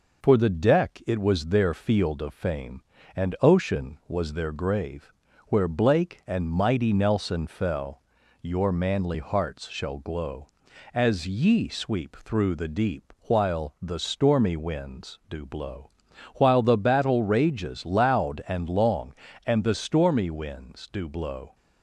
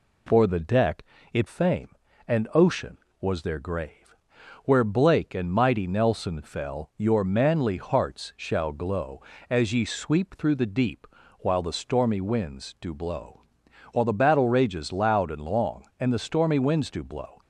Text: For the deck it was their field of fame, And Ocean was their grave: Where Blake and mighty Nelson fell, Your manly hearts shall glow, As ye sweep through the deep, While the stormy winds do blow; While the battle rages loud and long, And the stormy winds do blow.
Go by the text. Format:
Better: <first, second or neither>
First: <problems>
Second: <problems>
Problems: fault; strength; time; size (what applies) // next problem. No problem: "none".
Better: first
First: none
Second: pauses between "deck" and "it"; slight; at 1.0 s; 0.26 s long // skips "was their field of"; at 1.4 s